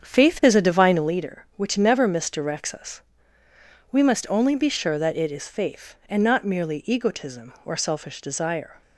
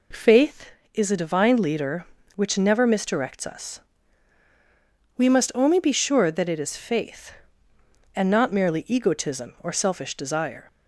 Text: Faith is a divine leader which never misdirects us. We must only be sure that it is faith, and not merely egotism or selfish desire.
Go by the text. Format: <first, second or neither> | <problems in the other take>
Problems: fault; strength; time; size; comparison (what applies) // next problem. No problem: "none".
second | starts louder than the rest; strong; until 1.1 s; 7.5 dB